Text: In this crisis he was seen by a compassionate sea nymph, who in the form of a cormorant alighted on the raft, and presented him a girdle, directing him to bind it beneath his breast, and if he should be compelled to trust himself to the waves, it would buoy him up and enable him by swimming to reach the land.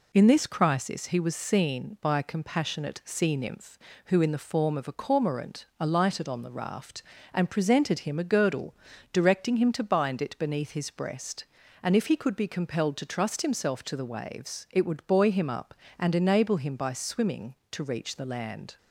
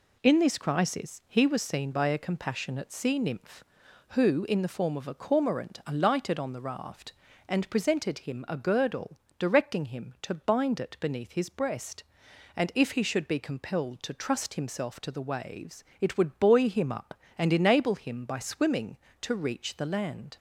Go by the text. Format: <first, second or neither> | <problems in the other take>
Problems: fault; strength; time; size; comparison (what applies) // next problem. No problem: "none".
second | says "could" for "should"; at 12.1 s